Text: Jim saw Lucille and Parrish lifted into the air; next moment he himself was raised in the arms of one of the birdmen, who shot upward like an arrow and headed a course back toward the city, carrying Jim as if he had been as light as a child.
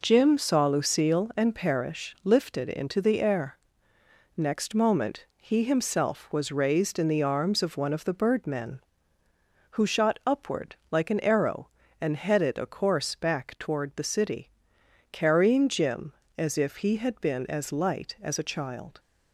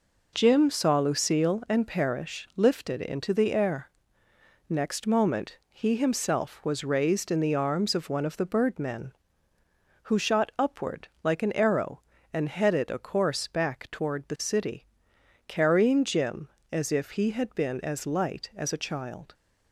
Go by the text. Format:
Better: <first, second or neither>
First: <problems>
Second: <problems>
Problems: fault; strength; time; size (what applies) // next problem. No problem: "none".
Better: neither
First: pauses between "upward" and "like"; slight; at 10.7 s; 0.16 s long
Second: pauses between "upward" and "like"; slight; at 11.0 s; 0.16 s long